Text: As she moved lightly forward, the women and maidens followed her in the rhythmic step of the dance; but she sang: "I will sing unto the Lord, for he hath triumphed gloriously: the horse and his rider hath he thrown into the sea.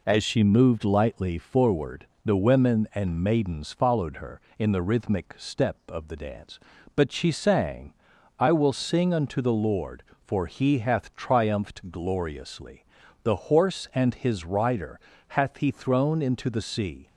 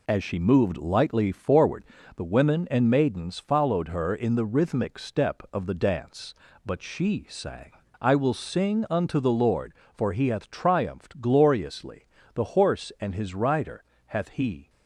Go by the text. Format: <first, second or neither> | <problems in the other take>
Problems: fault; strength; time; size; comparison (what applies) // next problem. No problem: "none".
first | pauses between "rider" and "hath"; slight; at 13.8 s; 0.26 s long; slight in the first // stops before "thrown into the sea"; at 14.6 s